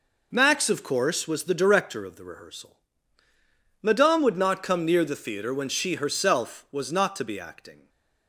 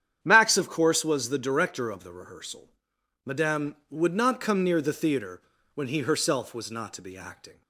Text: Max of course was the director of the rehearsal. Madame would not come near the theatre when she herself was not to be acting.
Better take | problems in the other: first | starts louder than the rest; strong; until 1.2 s; 9 dB // pauses between "theatre" and "when"; slight; at 5.4 s; 0.32 s long // says "he" for "she"; at 5.8 s

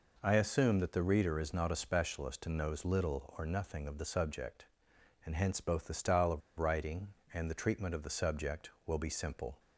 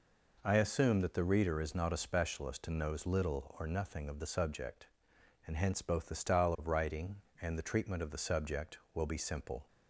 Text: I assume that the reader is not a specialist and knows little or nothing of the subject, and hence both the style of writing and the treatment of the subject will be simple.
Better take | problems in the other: second | pauses between "of" and "writing"; slight; at 6.4 s; 0.18 s long

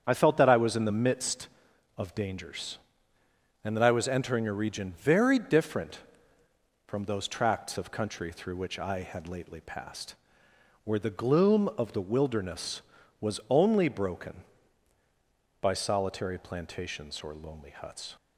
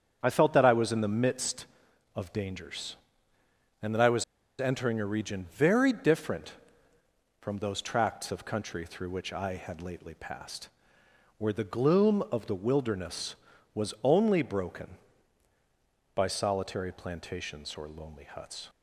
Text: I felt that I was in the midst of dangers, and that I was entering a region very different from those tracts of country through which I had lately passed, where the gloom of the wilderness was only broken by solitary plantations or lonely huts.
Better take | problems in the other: first | starts louder than the rest; strong; until 1.2 s; 8 dB; strong in the first // pauses between "was" and "entering"; slight; at 4.2 s; 0.35 s long

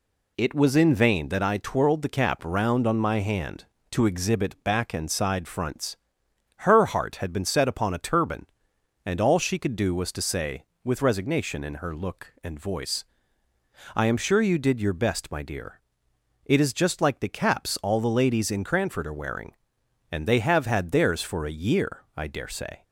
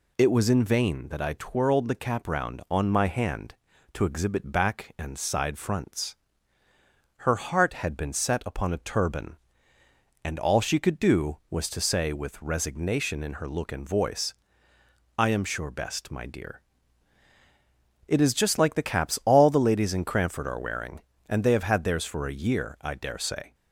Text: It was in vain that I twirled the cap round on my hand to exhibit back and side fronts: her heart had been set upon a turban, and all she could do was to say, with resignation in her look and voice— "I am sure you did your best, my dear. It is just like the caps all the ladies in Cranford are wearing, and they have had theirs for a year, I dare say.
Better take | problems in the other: first | skips "you did your"; at 15.7 s

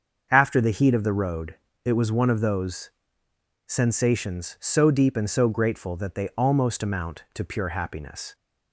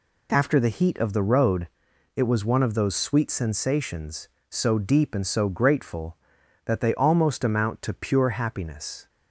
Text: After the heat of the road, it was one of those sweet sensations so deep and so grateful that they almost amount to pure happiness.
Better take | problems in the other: second | starts louder than the rest; until 1.3 s; 6.5 dB // skips "sweet"; at 3.2 s

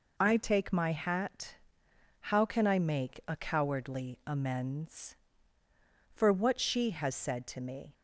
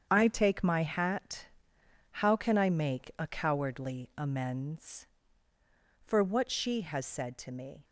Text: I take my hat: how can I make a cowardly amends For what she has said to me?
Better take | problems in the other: first | gets quieter; strong; throughout; 9.5 dB

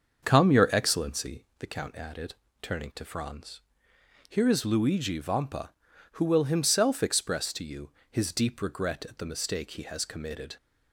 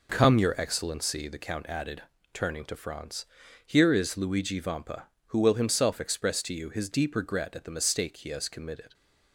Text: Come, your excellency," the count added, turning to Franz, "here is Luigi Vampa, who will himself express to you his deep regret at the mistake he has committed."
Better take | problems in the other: second | starts louder than the rest; until 1.7 s; 6.5 dB // pauses between "you" and "his"; slight; at 7.9 s; 0.20 s long

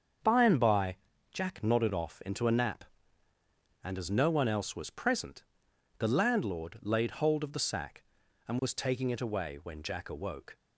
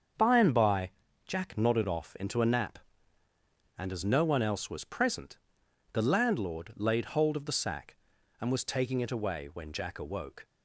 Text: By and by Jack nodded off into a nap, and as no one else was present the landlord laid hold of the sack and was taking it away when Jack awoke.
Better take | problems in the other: neither | starts louder than the rest; the same in both // pauses between "by" and "Jack"; slight; the same in both // pauses between "present" and "the"; noticeable; the same in both

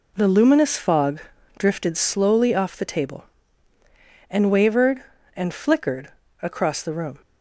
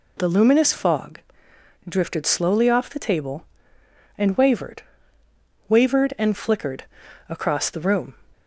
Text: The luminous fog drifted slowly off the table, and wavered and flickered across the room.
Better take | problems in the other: first | pauses between "fog" and "drifted"; noticeable; at 1.1 s; 0.68 s long; also in the first // says "wavered" twice; at 5.6 s // pauses between "flickered" and "across"; at 6.8 s; 0.42 s long; slight in the first

